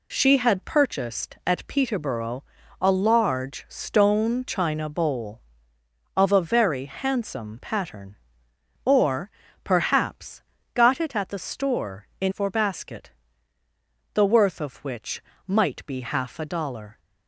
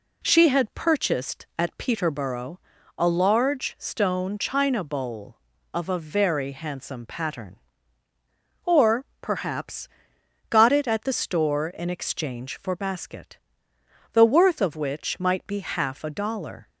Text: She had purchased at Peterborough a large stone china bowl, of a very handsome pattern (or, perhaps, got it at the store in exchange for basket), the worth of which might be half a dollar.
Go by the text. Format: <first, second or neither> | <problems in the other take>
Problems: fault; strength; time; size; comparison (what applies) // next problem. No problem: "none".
second | pauses between "Peterborough" and "a"; at 2.4 s; 0.38 s long; slight in the second // skips "exchange"; at 12.3 s // pauses between "which" and "might"; slight; at 15.2 s; 0.24 s long